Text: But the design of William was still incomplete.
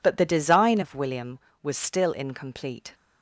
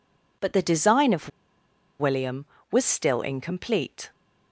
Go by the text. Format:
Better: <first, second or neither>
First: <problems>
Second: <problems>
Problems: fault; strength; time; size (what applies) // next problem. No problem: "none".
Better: first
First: none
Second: pauses between "of" and "William"; noticeable; at 1.2 s; 0.71 s long